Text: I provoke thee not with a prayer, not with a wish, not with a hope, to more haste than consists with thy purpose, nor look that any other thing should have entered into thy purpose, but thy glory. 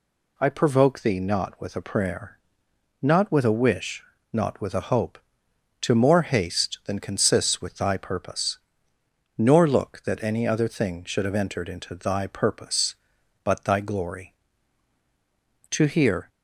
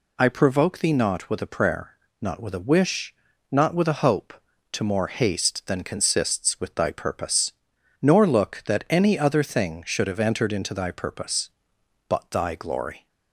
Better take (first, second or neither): second